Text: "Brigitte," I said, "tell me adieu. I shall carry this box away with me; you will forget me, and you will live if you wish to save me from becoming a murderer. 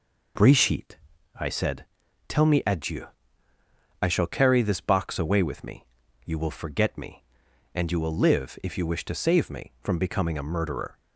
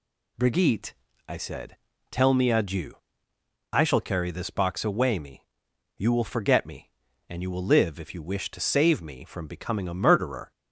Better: first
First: none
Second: skips "with"; at 5.1 s

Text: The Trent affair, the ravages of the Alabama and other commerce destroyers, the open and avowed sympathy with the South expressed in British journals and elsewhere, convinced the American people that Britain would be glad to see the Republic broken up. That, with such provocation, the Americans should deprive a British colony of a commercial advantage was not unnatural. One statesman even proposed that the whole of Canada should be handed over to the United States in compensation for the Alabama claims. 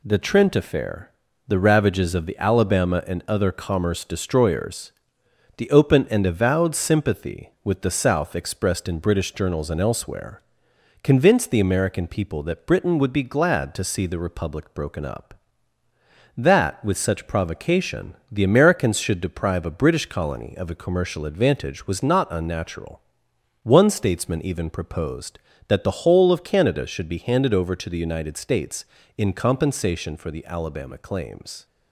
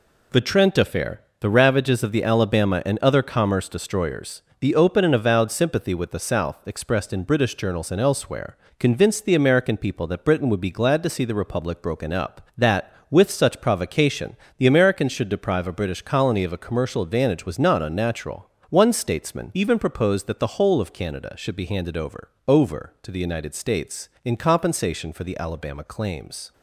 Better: first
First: none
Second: says "over" twice; at 22.4 s

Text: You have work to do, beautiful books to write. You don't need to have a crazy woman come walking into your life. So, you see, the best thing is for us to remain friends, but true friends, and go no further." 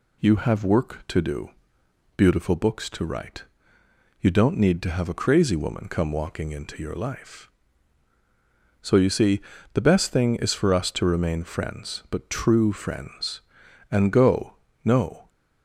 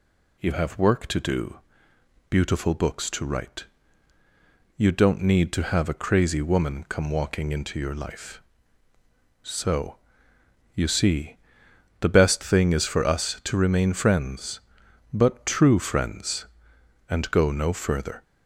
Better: second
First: pauses between "go" and "no"; slight; at 14.5 s; 0.28 s long // stops before "further"; at 15.2 s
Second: none

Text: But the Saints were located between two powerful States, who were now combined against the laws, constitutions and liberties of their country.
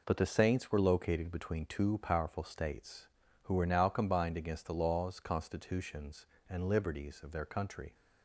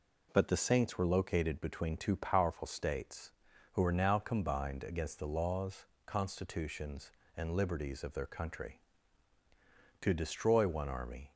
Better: first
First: none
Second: goes on to say "To destroy one army"; noticeable; from 10.0 s on; 1.3 s long

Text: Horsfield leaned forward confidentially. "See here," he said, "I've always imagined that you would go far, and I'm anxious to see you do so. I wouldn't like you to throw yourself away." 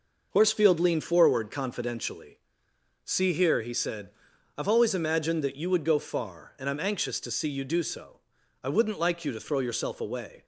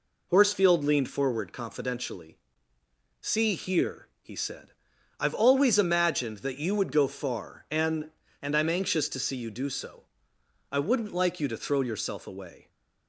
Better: first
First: none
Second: says "and" twice; at 8.4 s

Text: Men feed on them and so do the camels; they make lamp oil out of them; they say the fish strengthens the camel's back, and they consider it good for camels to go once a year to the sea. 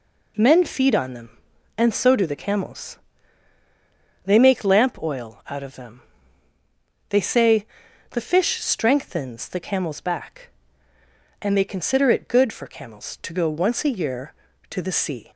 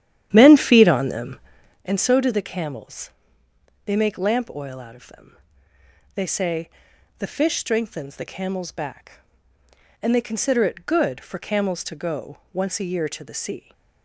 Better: first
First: pauses between "say" and "the"; at 7.6 s; 0.44 s long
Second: starts louder than the rest; strong; until 1.8 s; 10.5 dB // pauses between "say" and "the"; noticeable; at 6.6 s; 0.48 s long // pauses between "go" and "once"; slight; at 12.3 s; 0.16 s long

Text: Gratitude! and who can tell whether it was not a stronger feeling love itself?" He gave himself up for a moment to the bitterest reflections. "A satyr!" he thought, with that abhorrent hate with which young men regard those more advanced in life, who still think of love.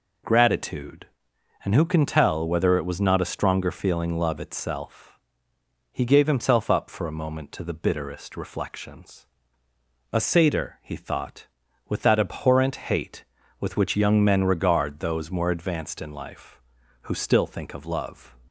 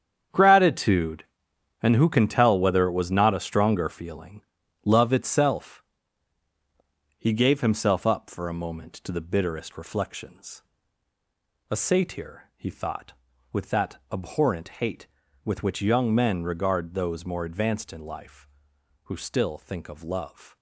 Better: first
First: none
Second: gets quieter; strong; throughout; 11.5 dB // pauses between "feeling" and "love"; at 4.4 s; 0.40 s long // pauses between "that" and "abhorrent"; slight; at 13.9 s; 0.16 s long

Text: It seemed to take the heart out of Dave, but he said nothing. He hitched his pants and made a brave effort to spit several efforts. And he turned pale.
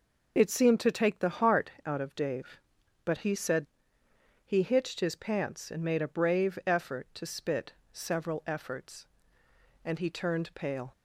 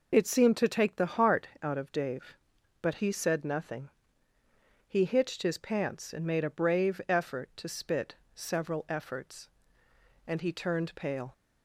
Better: second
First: skips "nothing"; at 4.0 s // pauses between "spit" and "several"; slight; at 7.7 s; 0.22 s long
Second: pauses between "spit" and "several"; slight; at 8.1 s; 0.22 s long

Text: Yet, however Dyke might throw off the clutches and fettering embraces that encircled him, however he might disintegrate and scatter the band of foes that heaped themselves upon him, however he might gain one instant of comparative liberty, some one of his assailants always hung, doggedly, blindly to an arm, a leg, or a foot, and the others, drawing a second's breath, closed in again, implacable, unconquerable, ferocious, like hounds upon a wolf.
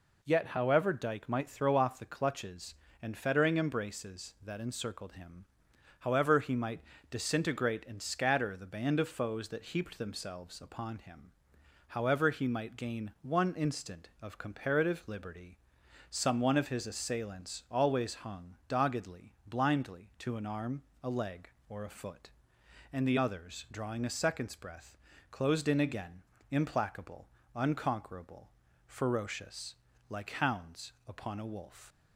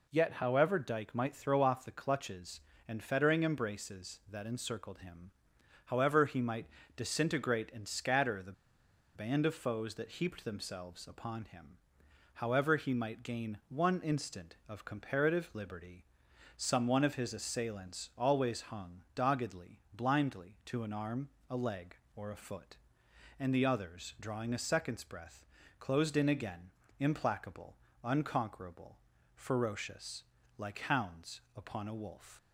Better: first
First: pauses between "might" and "disintegrate"; slight; at 6.7 s; 0.30 s long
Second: pauses between "might" and "disintegrate"; slight; at 6.6 s; 0.30 s long // pauses between "the" and "band"; noticeable; at 8.5 s; 0.63 s long

